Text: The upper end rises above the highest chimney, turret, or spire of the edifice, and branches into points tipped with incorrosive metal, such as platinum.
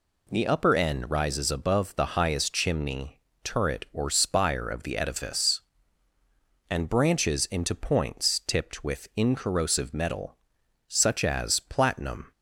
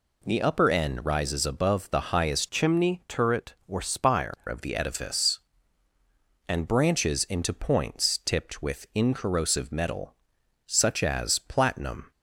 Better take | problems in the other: first | changes voice from "chimney" to "spire"; from 2.5 to 4.3 s; 1.8 s long

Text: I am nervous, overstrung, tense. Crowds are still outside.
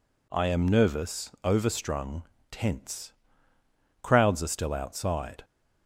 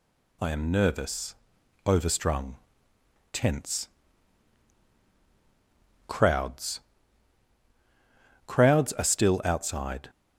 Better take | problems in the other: first | says "Crowds" twice; at 8.4 s

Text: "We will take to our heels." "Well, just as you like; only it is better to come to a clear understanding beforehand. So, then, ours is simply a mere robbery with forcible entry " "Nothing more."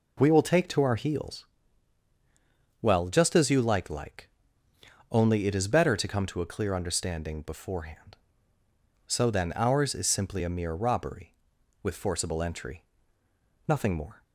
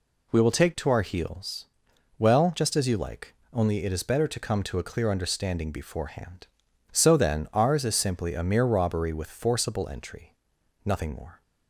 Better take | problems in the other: second | says "like" twice; at 3.8 s

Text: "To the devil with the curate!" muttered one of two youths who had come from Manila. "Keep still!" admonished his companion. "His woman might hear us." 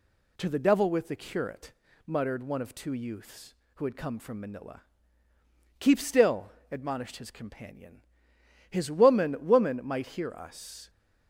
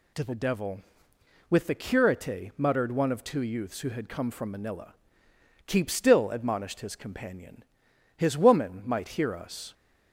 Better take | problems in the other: second | says "woman" twice; at 9.4 s

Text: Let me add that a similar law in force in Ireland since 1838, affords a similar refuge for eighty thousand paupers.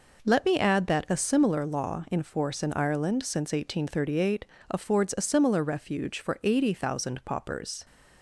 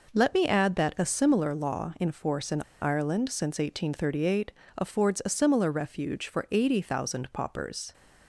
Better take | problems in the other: first | pauses between "in" and "Ireland"; slight; at 2.6 s; 0.19 s long

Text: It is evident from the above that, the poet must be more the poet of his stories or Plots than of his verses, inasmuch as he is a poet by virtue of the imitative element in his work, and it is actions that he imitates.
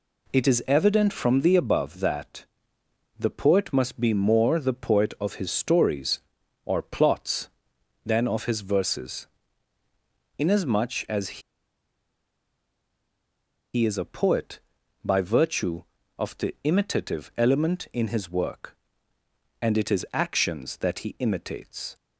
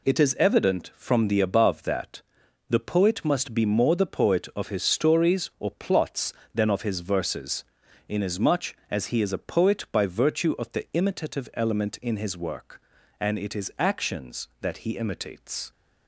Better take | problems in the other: second | pauses between "as" and "he"; strong; at 11.3 s; 2.3 s long

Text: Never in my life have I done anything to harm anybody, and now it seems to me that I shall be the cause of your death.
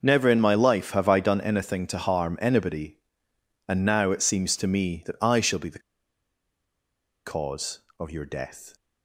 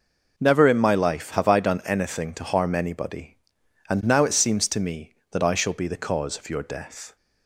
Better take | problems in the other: second | pauses between "the" and "cause"; strong; at 5.8 s; 1.4 s long

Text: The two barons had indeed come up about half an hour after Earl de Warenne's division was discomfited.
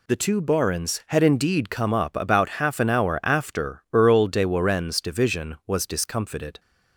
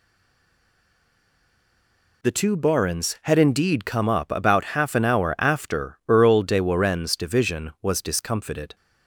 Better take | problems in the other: first | stays silent before the first word; until 2.2 s; 2.2 s long

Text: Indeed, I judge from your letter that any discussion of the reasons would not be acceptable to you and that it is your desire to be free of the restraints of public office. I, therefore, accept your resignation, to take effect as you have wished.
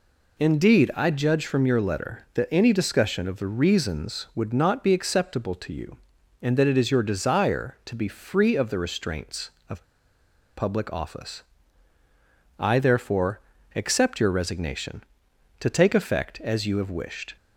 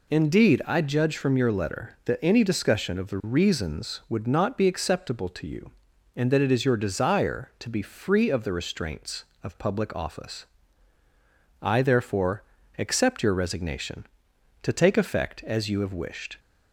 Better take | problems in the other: second | pauses between "of" and "public"; noticeable; at 9.8 s; 0.71 s long

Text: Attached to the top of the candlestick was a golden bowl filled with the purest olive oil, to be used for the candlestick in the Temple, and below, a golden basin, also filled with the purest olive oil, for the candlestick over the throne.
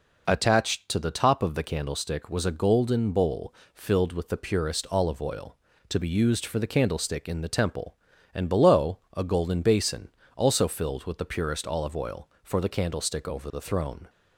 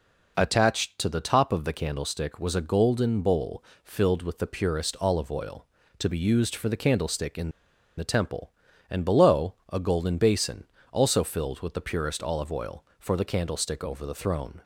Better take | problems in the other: first | pauses between "bowl" and "filled"; slight; at 3.6 s; 0.22 s long; slight in the first // pauses between "in" and "the"; noticeable; at 7.5 s; 0.46 s long

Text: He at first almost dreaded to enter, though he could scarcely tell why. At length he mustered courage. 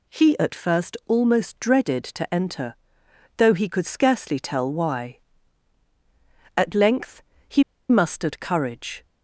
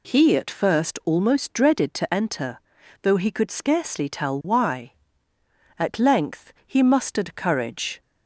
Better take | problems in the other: second | pauses between "length" and "he"; slight; at 7.2 s; 0.26 s long // pauses between "he" and "mustered"; slight; at 7.6 s; 0.26 s long

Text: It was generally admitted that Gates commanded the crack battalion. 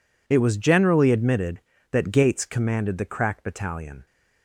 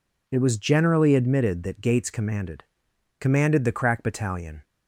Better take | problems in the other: first | says "commanded" twice; at 3.1 s

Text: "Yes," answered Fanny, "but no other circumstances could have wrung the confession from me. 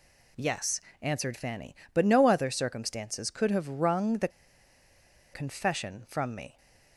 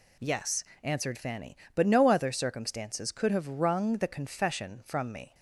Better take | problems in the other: second | pauses between "the" and "confession"; at 4.2 s; 1.0 s long

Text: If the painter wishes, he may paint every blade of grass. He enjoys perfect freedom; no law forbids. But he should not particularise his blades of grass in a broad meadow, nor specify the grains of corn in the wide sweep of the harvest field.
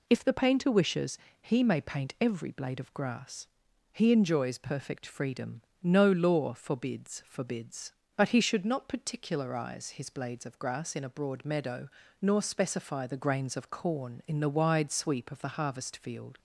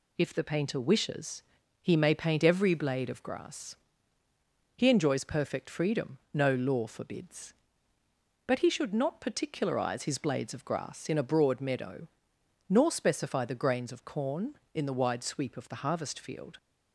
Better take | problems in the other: second | says "forbids" twice; at 7.2 s

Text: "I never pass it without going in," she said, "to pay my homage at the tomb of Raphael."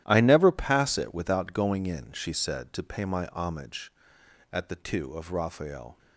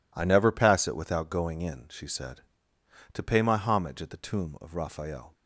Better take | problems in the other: second | starts louder than the rest; strong; until 1.0 s; 12.5 dB // says "two" for "tomb"; at 4.7 s

